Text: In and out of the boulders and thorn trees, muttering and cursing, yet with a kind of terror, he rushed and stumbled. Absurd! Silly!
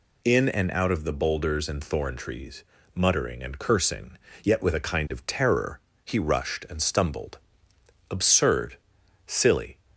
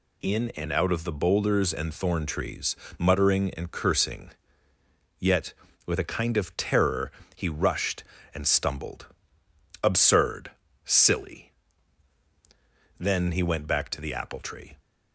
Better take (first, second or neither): first